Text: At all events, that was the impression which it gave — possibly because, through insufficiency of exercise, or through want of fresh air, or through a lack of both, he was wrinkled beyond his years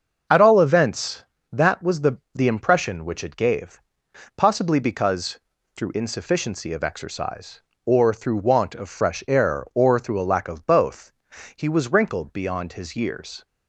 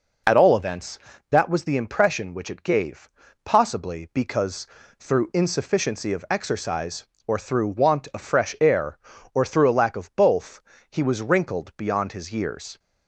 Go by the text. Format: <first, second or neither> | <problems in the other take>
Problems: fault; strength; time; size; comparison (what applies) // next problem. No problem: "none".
second | starts louder than the rest; until 1.6 s; 6.5 dB // says "the" twice; at 2.3 s